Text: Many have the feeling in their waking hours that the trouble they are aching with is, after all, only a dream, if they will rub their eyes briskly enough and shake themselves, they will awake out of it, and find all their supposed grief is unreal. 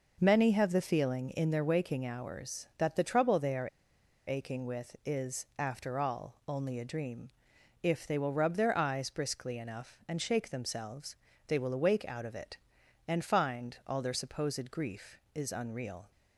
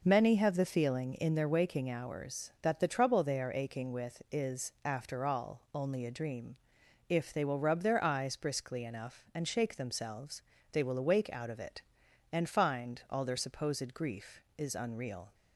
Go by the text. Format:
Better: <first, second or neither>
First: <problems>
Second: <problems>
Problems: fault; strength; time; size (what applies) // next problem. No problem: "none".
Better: second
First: pauses between "are" and "aching"; noticeable; at 3.6 s; 0.58 s long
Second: none